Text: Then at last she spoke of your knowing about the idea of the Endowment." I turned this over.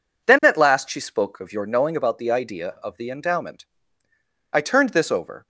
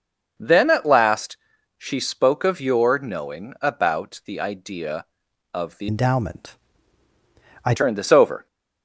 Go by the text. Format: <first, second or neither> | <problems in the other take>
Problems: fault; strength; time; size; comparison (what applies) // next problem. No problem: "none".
first | pauses between "last" and "she"; at 1.3 s; 0.42 s long // changes voice from "Endowment" to "I"; from 5.8 to 7.7 s; 1.9 s long